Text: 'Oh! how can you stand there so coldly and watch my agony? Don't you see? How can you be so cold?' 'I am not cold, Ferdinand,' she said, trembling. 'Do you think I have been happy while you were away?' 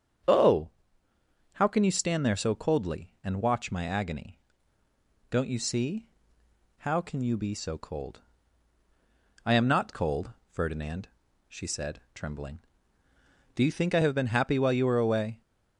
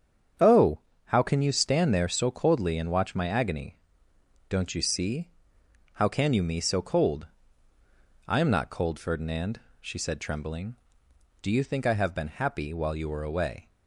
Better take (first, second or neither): first